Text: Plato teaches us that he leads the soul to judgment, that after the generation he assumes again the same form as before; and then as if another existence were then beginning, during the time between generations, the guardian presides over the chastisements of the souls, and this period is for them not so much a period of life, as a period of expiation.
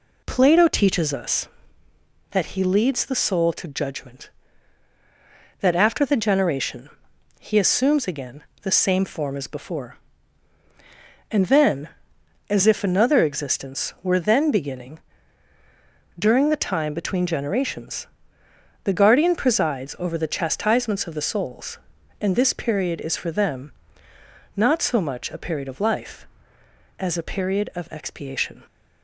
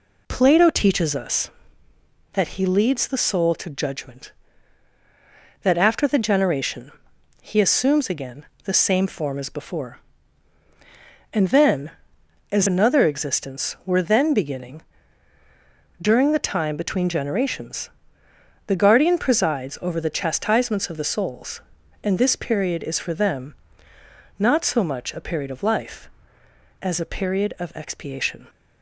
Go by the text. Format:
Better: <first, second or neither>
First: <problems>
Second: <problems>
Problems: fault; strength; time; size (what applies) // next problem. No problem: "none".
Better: first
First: pauses between "generation" and "he"; noticeable; at 6.8 s; 0.50 s long // pauses between "again" and "the"; slight; at 8.4 s; 0.20 s long // pauses between "them" and "not"; noticeable; at 23.7 s; 0.86 s long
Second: pauses between "generation" and "he"; noticeable; at 6.9 s; 0.50 s long // pauses between "again" and "the"; slight; at 8.4 s; 0.20 s long // skips "if"; at 12.6 s // pauses between "them" and "not"; noticeable; at 23.5 s; 0.86 s long